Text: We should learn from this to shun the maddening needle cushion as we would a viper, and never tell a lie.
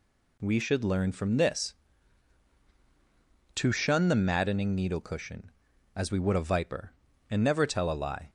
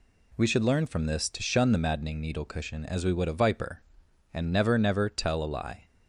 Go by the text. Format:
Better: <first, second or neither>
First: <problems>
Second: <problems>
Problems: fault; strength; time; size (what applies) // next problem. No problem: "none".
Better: first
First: none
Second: says "never" twice; at 4.7 s